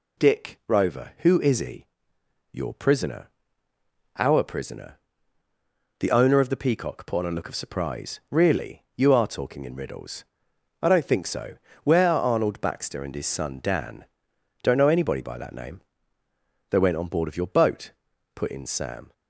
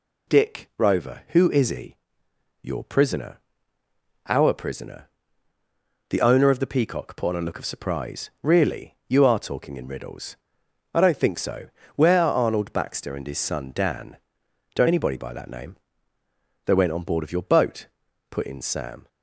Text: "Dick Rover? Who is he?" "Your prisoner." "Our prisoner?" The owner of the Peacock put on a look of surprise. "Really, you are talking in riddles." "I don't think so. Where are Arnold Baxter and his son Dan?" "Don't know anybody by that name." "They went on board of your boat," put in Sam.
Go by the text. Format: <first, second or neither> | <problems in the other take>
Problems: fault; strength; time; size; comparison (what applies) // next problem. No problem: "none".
first | skips "know"; at 14.8 s